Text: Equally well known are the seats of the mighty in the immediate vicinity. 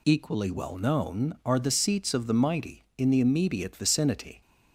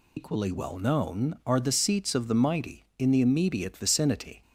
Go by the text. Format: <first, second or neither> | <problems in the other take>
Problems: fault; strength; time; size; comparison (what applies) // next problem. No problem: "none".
first | loses the start of "Equally"; at 0.1 s; 100 ms